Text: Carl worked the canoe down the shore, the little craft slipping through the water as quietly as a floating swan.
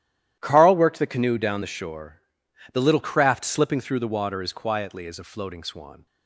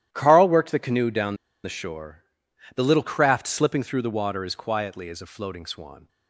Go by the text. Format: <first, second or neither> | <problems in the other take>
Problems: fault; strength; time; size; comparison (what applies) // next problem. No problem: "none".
first | starts louder than the rest; strong; until 1.1 s; 12 dB; strong in the first // pauses between "down" and "the"; slight; at 1.3 s; 0.27 s long